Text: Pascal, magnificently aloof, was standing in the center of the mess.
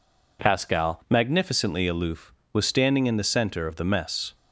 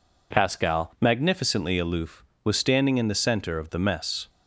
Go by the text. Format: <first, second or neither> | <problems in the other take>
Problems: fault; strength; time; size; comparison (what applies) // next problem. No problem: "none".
neither | none